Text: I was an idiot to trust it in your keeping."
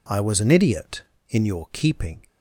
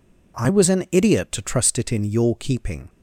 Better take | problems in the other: second | skips "to trust it"; at 1.1 s

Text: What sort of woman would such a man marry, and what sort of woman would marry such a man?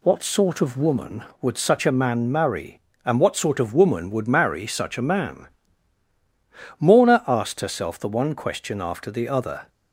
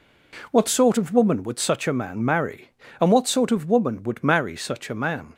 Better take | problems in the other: second | goes on to say "Morna asked herself the one question after the other"; strong; from 6.7 s on; 2.9 s long

